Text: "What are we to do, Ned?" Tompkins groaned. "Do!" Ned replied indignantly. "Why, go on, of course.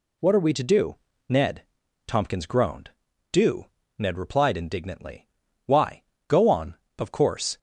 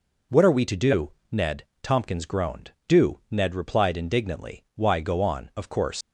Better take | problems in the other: first | leaves "course" unfinished; at 6.0 s; 120 ms

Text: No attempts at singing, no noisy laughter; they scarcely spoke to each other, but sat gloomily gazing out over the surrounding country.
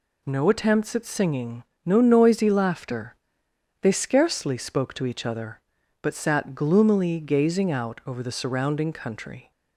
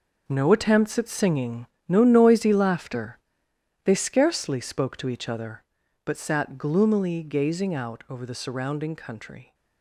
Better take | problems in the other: first | gets quieter; strong; throughout; 10.5 dB

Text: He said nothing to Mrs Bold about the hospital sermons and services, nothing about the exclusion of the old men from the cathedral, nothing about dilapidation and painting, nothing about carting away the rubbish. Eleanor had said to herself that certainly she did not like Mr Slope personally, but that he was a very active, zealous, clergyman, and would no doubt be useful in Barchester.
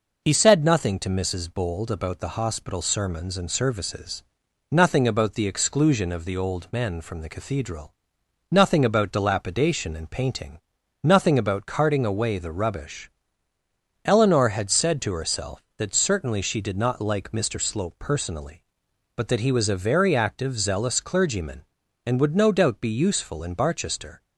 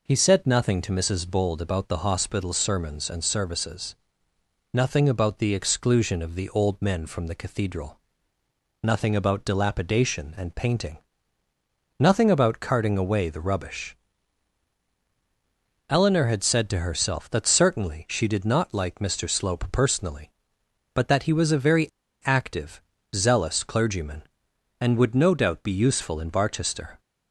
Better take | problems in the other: first | pauses between "very" and "active"; at 21.8 s; 0.37 s long

